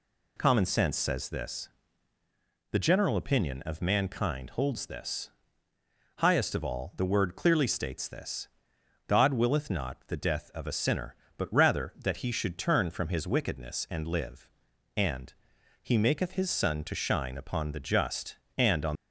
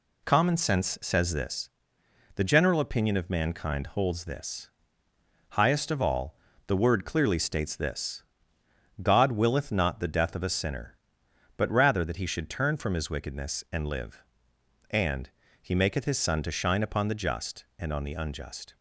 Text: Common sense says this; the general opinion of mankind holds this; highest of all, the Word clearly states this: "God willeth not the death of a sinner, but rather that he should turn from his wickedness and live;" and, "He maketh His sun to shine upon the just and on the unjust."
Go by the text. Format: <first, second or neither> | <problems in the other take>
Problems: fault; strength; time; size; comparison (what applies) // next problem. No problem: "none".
second | stops before "the unjust"; at 18.9 s